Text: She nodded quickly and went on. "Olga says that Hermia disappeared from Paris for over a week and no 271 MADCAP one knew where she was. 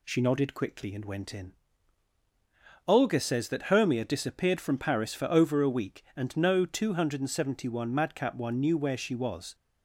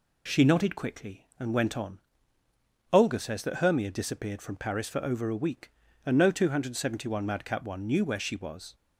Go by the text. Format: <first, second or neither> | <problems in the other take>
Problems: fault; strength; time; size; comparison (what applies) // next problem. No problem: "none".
second | says "in" for "on"; at 1.3 s